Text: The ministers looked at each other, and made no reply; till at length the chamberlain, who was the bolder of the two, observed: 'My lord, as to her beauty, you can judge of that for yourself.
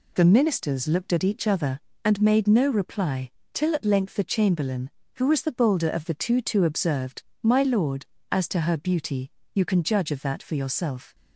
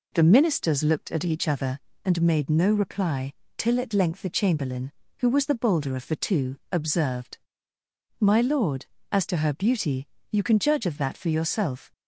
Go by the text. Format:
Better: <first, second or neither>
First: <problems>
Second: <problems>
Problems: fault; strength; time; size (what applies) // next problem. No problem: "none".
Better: second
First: says "two" twice; at 6.3 s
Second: none